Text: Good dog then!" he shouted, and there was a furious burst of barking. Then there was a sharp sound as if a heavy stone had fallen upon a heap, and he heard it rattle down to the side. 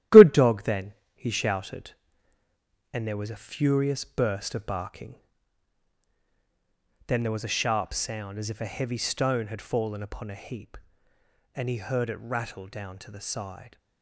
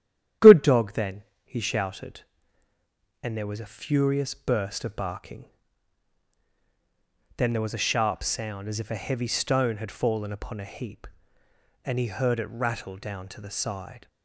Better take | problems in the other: second | gets quieter; throughout; 6 dB // starts louder than the rest; strong; until 1.3 s; 13 dB; strong in the second

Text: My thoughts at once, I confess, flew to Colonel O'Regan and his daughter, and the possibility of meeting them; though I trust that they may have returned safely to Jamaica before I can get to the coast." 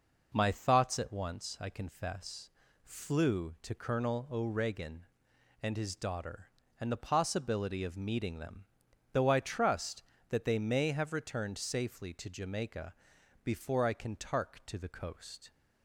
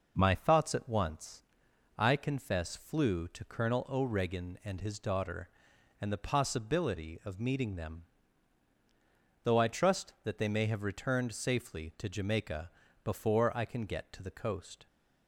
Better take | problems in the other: second | pauses between "Jamaica" and "before"; noticeable; at 12.9 s; 0.48 s long; slight in the second // says "tark" for "get"; at 14.1 s

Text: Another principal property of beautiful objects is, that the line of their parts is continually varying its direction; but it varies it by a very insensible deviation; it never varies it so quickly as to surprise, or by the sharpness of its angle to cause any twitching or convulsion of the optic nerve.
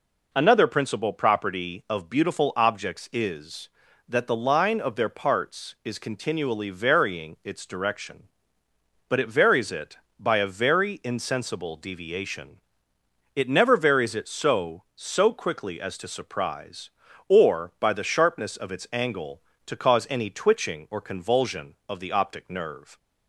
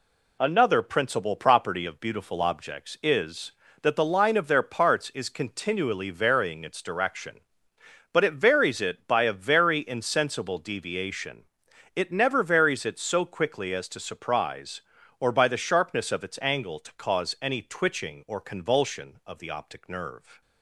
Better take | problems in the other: second | says "so" twice; at 14.9 s

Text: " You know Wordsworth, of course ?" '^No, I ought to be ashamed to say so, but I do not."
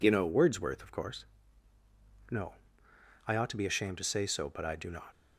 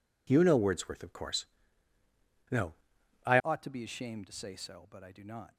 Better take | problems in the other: first | changes voice at "ought"; from 3.4 s on; 2.1 s long

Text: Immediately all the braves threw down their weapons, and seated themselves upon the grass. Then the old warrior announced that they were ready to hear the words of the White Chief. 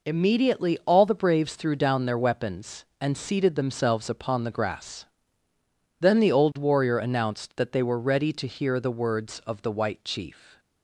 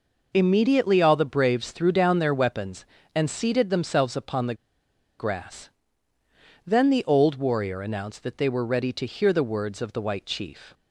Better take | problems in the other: first | pauses between "the" and "grass"; noticeable; at 4.5 s; 0.64 s long

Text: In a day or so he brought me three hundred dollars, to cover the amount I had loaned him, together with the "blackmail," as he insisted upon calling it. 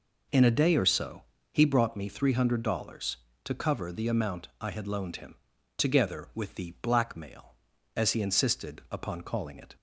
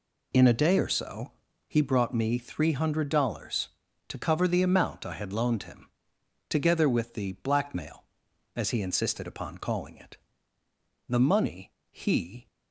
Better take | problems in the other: first | pauses between "so" and "he"; slight; at 1.3 s; 0.34 s long; slight in the first // goes on to say "The money he"; from 11.0 s on; 1.3 s long

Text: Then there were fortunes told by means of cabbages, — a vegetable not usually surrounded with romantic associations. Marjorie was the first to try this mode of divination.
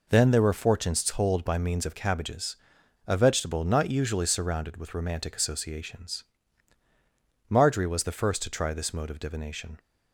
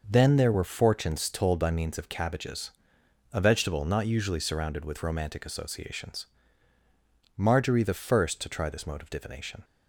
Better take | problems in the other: first | skips "was"; at 7.8 s

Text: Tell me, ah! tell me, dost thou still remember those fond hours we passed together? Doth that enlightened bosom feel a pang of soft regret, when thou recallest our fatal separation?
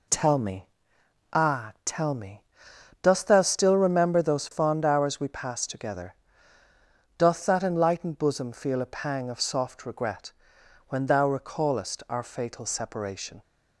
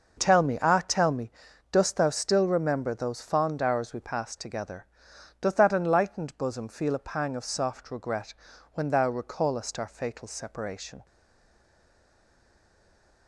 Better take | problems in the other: first | stays silent after the last word; from 11.0 s on; 2.2 s long

